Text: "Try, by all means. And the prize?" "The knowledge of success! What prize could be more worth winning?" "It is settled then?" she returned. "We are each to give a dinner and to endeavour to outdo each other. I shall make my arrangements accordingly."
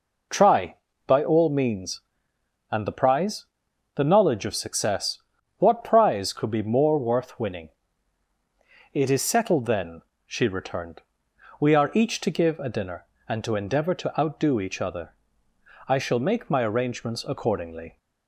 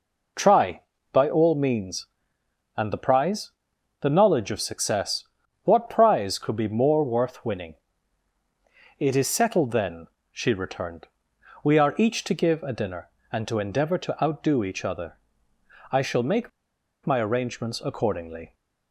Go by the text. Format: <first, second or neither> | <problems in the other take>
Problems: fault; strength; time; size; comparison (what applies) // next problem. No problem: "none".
first | pauses between "make" and "my"; noticeable; at 16.4 s; 0.55 s long